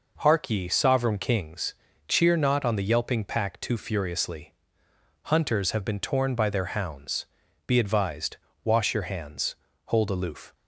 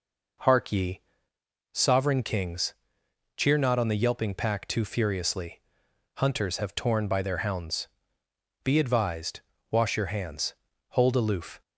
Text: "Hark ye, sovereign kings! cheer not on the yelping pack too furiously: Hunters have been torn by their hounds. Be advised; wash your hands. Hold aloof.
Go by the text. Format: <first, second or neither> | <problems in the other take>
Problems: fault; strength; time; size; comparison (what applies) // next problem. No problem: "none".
first | skips "been"; at 6.7 s